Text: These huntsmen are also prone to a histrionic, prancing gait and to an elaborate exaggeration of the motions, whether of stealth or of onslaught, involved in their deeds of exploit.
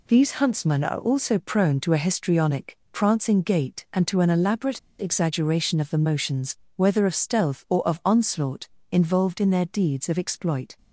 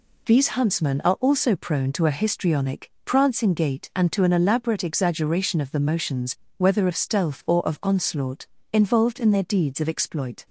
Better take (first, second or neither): second